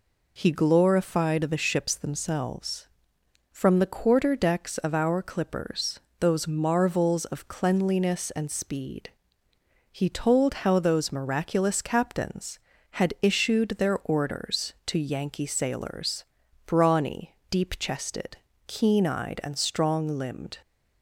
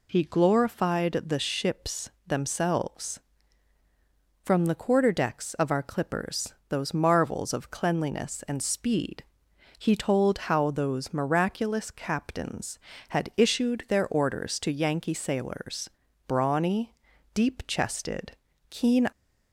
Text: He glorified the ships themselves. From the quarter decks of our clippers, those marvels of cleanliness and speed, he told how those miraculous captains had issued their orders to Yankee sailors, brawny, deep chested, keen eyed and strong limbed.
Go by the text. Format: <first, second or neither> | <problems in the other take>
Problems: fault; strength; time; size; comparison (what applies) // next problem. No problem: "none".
first | pauses between "ships" and "themselves"; slight; at 2.1 s; 0.16 s long // stops before "eyed and strong limbed"; at 19.1 s